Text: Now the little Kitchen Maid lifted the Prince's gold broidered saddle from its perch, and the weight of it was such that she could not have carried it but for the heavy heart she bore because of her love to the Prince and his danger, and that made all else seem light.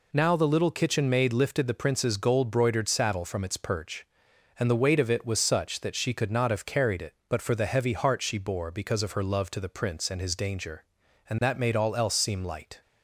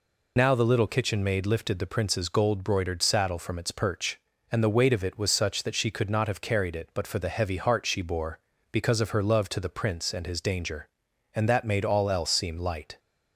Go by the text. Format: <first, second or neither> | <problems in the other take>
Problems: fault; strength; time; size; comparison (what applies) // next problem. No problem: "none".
first | loses the start of "Now"; at 0.3 s; 40 ms